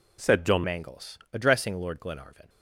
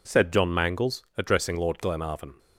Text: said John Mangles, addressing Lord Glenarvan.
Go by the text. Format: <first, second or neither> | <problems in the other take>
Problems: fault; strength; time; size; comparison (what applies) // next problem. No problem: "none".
second | changes voice at "Mangles"; from 0.6 s on; 1.8 s long